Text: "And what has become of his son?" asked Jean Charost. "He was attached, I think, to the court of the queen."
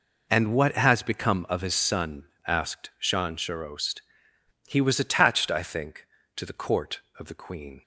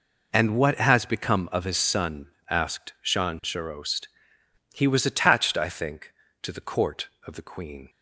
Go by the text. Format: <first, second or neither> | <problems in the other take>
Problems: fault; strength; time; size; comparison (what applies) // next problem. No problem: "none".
neither | none